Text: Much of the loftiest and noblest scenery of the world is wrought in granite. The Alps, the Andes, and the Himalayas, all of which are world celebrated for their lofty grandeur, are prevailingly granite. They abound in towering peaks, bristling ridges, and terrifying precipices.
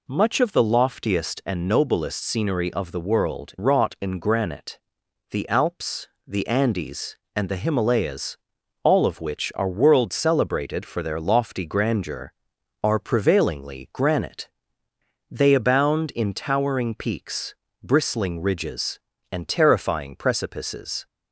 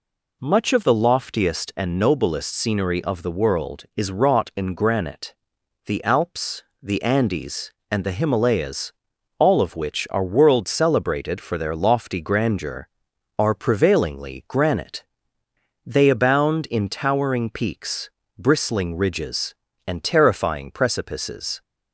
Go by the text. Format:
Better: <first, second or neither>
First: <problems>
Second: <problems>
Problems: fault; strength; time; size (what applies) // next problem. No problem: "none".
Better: second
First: skips "is"; at 3.5 s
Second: none